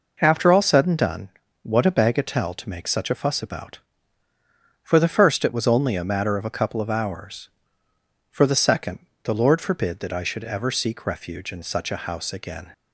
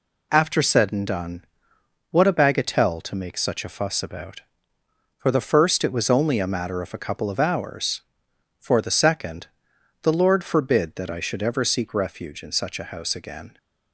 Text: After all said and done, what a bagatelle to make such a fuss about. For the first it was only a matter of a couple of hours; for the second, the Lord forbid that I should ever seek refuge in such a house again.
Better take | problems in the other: first | skips "all"; at 0.6 s

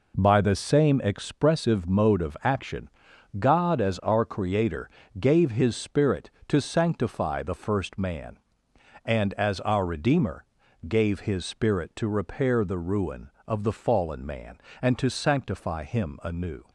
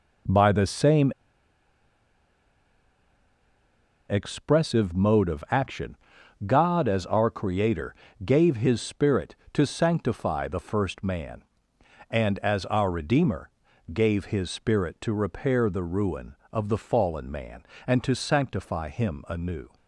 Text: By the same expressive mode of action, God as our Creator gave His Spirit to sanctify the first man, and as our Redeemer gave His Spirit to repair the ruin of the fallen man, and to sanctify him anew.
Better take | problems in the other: first | pauses between "same" and "expressive"; strong; at 1.1 s; 2.9 s long // pauses between "Creator" and "gave"; slight; at 7.9 s; 0.30 s long; slight in the first // pauses between "Redeemer" and "gave"; at 13.4 s; 0.44 s long; also in the first

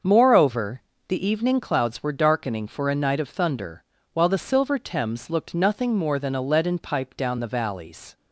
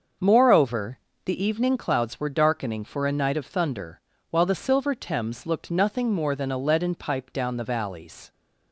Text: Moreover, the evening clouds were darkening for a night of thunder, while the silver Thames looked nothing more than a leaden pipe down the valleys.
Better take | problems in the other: neither | starts louder than the rest; the same in both

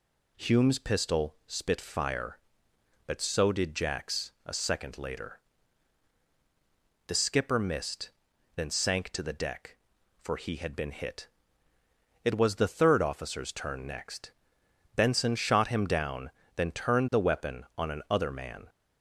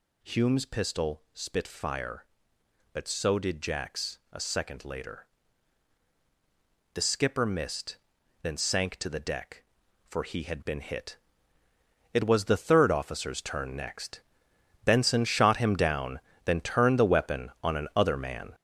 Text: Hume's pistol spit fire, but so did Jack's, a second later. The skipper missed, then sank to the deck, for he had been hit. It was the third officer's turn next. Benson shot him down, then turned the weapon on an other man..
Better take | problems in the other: first | gets louder; strong; throughout; 7.5 dB

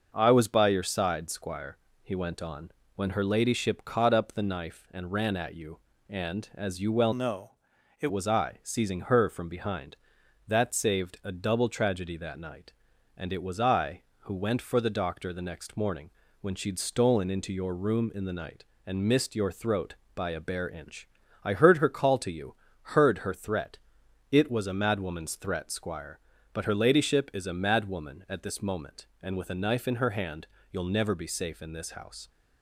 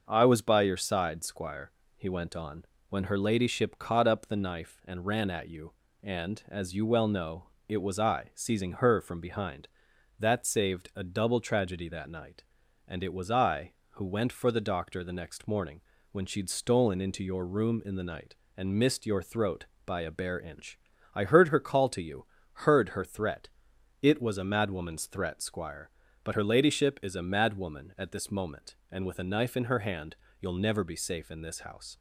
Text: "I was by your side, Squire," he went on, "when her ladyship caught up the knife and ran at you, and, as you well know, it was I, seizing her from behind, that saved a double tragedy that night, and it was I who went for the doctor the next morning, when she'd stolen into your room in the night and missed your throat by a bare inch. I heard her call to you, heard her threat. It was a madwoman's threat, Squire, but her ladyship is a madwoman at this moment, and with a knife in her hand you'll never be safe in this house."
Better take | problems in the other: second | starts louder than the rest; noticeable; until 1.1 s; 6 dB; also in the second // changes voice from "know" to "it"; from 7.1 to 8.0 s; 0.9 s long // pauses between "hand" and "you'll"; slight; at 30.4 s; 0.24 s long; slight in the second

